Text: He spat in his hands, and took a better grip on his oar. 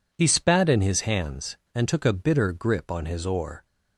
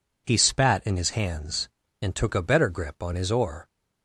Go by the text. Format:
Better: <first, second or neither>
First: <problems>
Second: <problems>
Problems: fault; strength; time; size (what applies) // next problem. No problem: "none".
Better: second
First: says "bitter" for "better"; at 2.1 s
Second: none